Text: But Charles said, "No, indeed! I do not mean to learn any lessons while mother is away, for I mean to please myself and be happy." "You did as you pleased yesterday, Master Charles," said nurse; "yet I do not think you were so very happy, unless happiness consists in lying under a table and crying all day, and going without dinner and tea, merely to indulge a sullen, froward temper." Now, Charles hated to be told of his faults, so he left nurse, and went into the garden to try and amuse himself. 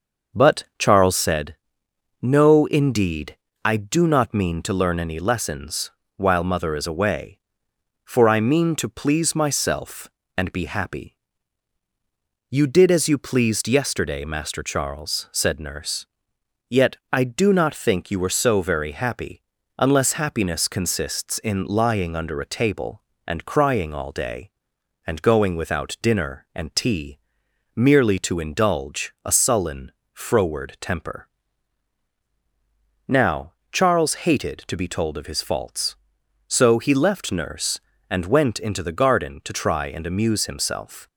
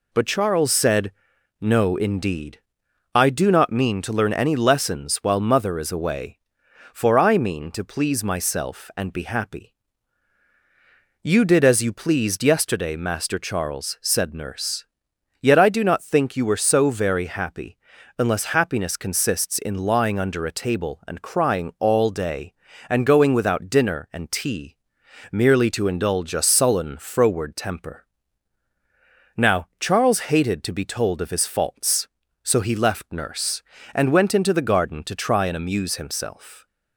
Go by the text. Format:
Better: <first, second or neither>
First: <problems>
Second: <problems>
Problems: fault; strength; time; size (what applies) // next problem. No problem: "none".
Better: second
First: starts louder than the rest; noticeable; until 1.2 s; 6 dB // pauses between "lessons" and "while"; slight; at 5.9 s; 0.26 s long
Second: none